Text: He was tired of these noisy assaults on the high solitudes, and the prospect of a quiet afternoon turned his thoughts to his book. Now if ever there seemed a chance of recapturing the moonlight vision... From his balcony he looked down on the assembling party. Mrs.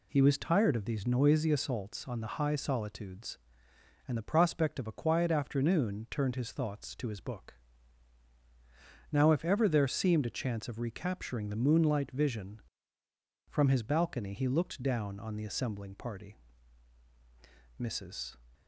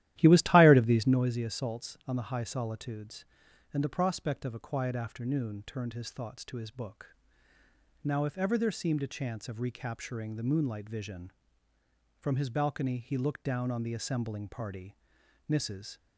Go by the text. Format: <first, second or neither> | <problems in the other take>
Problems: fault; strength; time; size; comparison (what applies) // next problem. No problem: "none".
first | starts louder than the rest; strong; until 1.3 s; 13.5 dB